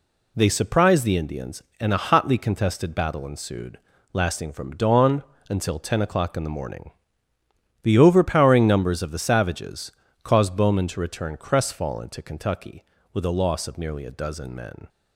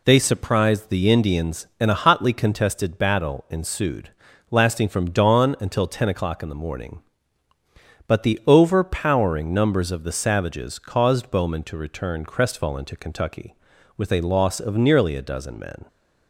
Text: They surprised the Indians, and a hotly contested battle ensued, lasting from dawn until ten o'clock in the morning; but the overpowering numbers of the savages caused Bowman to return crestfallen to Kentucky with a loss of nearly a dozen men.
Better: second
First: pauses between "dawn" and "until"; slight; at 5.2 s; 0.26 s long // skips "but"; at 7.3 s // pauses between "savages" and "caused"; slight; at 9.9 s; 0.32 s long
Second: none

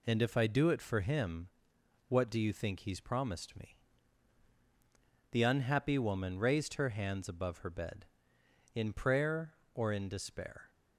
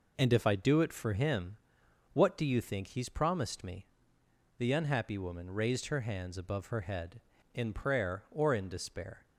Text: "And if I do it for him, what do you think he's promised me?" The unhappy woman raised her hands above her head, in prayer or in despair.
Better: second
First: says "bed" for "head"; at 7.7 s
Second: none

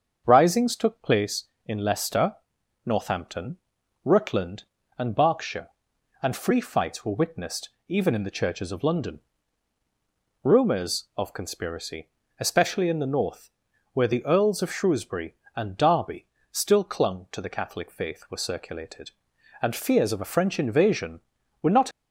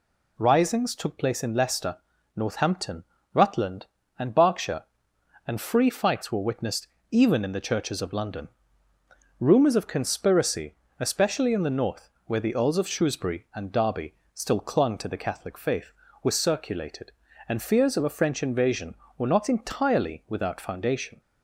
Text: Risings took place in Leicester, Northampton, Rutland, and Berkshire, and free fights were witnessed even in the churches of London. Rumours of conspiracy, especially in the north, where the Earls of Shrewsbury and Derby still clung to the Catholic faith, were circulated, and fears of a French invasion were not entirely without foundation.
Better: second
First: starts louder than the rest; until 1.2 s; 7 dB // pauses between "witnessed" and "even"; slight; at 7.6 s; 0.18 s long // pauses between "Derby" and "still"; slight; at 16.2 s; 0.24 s long // stops before "entirely without foundation"; at 21.9 s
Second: pauses between "witnessed" and "even"; slight; at 6.8 s; 0.22 s long // pauses between "Derby" and "still"; slight; at 14.1 s; 0.20 s long

